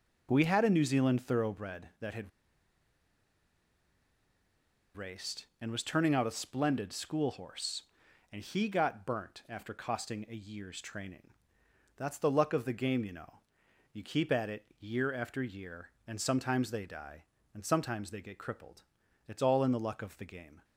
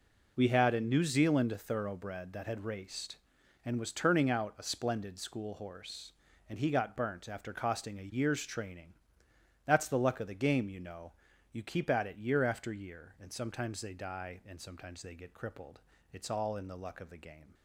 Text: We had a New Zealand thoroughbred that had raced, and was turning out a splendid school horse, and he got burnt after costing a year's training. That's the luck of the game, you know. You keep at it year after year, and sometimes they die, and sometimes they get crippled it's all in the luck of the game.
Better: second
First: pauses between "had" and "raced"; strong; at 2.3 s; 2.6 s long // pauses between "crippled" and "it's"; at 18.8 s; 0.44 s long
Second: pauses between "crippled" and "it's"; slight; at 15.7 s; 0.34 s long

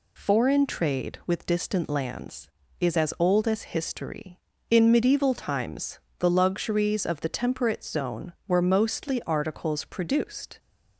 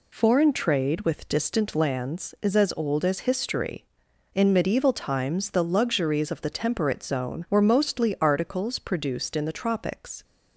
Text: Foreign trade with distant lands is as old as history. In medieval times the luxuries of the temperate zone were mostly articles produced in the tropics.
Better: second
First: pauses between "times" and "the"; slight; at 5.9 s; 0.20 s long // stops before "in the tropics"; at 10.5 s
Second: none

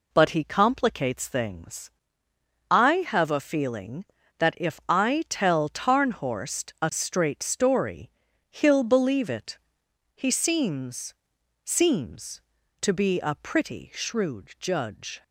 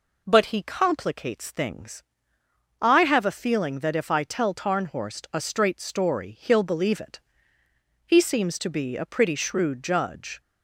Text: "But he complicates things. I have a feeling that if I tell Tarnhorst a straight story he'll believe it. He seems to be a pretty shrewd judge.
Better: second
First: pauses between "story" and "he'll"; at 8.1 s; 0.40 s long // says "seems" twice; at 11.6 s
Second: none

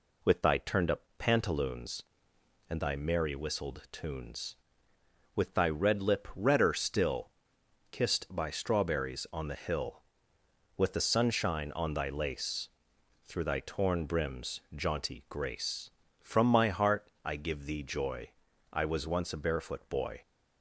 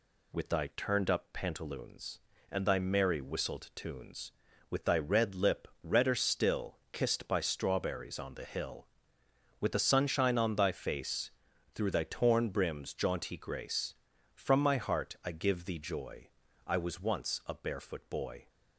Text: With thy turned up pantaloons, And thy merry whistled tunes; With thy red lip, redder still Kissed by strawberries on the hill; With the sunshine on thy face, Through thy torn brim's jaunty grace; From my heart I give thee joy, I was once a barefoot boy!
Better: second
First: pauses between "up" and "pantaloons"; slight; at 1.0 s; 0.16 s long // pauses between "still" and "Kissed"; noticeable; at 7.3 s; 0.60 s long // says "lace" for "face"; at 12.0 s // pauses between "heart" and "I"; slight; at 17.0 s; 0.16 s long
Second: pauses between "still" and "Kissed"; slight; at 6.7 s; 0.16 s long

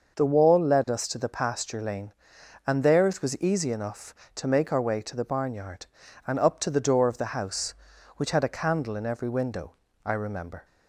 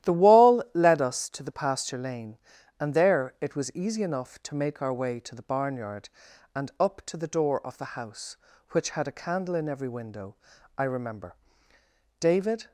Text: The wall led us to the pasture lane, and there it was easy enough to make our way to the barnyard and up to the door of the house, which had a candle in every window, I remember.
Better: first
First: none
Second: starts louder than the rest; strong; until 1.1 s; 13 dB // goes on to say "David"; from 12.1 s on; 0.52 s long

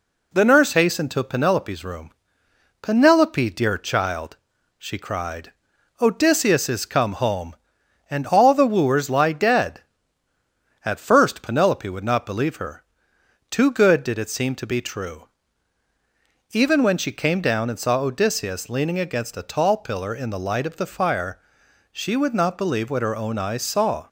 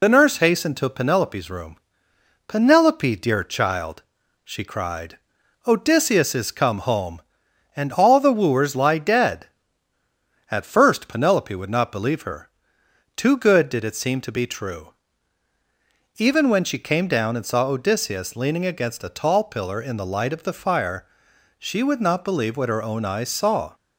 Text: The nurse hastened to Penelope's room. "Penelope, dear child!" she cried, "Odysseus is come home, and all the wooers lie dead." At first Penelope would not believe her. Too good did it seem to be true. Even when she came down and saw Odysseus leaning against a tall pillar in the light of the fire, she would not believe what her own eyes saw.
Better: first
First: none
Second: loses the start of "The"; at 0.0 s; 50 ms

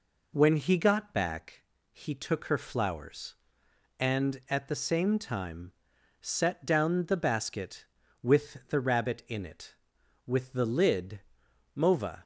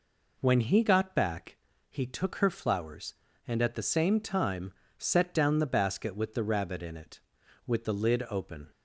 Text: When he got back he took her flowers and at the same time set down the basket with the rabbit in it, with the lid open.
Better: second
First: pauses between "back" and "he"; slight; at 1.6 s; 0.30 s long // pauses between "time" and "set"; noticeable; at 5.7 s; 0.50 s long // says "mova" for "open"; at 11.7 s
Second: pauses between "back" and "he"; slight; at 1.5 s; 0.32 s long // pauses between "time" and "set"; slight; at 4.7 s; 0.28 s long

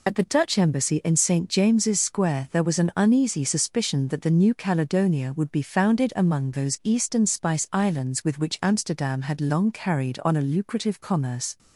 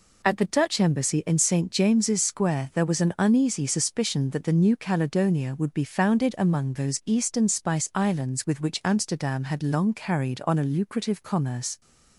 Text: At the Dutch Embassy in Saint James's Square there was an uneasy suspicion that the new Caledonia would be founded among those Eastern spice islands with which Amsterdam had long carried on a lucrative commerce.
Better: second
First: loses the start of "At"; at 0.0 s; 45 ms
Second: none

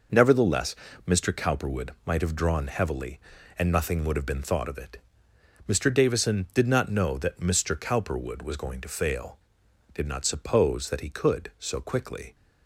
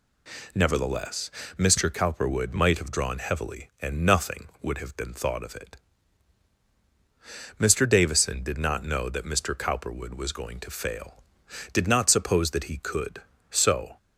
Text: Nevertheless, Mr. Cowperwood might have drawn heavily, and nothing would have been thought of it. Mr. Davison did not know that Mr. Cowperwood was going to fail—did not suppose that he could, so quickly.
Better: first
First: none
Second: stops before "quickly"; at 13.9 s

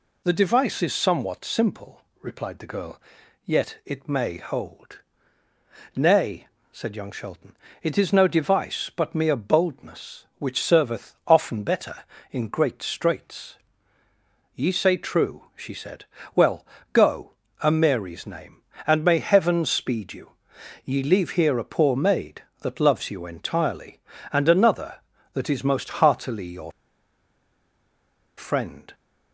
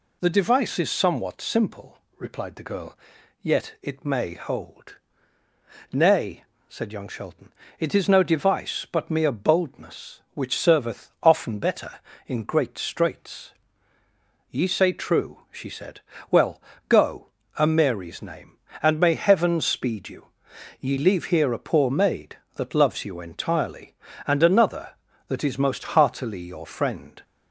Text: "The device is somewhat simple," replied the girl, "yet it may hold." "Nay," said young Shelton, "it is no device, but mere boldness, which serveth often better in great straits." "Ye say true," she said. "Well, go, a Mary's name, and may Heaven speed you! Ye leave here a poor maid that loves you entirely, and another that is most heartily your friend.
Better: second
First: pauses between "your" and "friend"; strong; at 26.7 s; 1.6 s long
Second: none

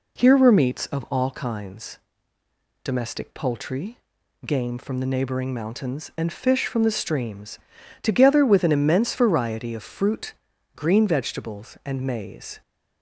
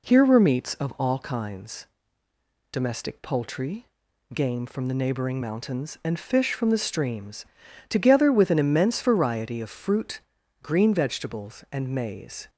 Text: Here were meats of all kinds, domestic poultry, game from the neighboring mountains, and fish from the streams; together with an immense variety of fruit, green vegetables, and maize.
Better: neither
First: none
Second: none

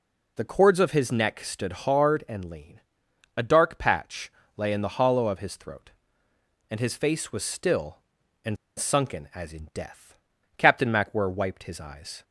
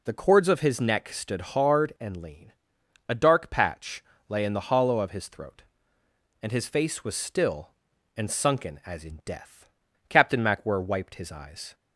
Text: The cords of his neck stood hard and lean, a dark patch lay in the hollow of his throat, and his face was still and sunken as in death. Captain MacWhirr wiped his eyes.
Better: second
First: pauses between "patch" and "lay"; slight; at 4.3 s; 0.26 s long // pauses between "and" and "sunken"; slight; at 8.5 s; 0.22 s long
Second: pauses between "patch" and "lay"; slight; at 4.0 s; 0.26 s long

